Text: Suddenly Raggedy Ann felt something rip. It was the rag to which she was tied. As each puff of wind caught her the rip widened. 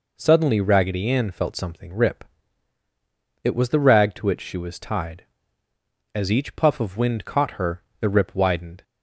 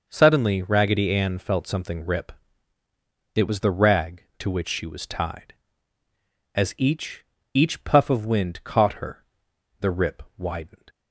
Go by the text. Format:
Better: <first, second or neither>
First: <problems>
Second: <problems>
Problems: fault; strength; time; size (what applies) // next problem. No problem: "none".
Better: first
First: pauses between "her" and "the"; slight; at 7.8 s; 0.18 s long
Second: says "each" twice; at 7.5 s // pauses between "her" and "the"; noticeable; at 9.2 s; 0.54 s long // pauses between "rip" and "widened"; slight; at 10.2 s; 0.16 s long